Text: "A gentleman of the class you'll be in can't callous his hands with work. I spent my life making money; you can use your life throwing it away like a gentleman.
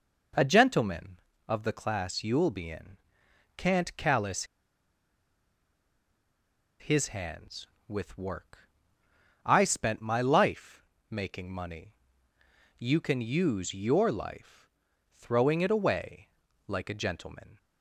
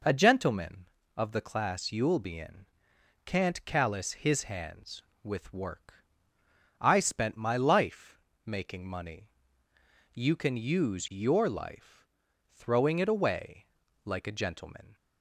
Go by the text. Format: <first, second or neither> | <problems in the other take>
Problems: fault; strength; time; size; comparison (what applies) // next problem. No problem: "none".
second | pauses between "in" and "can't"; noticeable; at 2.9 s; 0.60 s long; noticeable in the second // pauses between "callous" and "his"; strong; at 4.4 s; 2.3 s long // pauses between "life" and "making"; slight; at 10.8 s; 0.26 s long; slight in the second // pauses between "life" and "throwing"; noticeable; at 14.6 s; 0.48 s long; noticeable in the second // pauses between "away" and "like"; at 16.2 s; 0.40 s long; also in the second